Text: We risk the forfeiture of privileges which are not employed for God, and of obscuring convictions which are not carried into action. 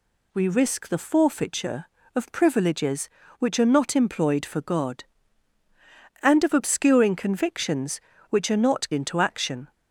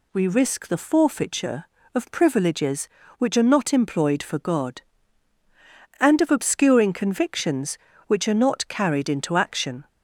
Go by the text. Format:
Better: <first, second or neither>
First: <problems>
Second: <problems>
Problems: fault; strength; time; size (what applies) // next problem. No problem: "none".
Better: second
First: skips "carried"; at 8.9 s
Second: none